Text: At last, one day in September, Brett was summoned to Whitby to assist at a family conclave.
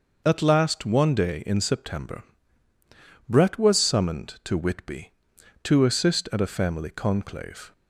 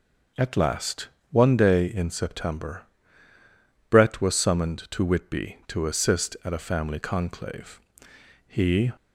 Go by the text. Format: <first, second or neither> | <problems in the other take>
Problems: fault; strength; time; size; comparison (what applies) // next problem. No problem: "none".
first | goes on to say "He"; slight; from 8.4 s on; 0.44 s long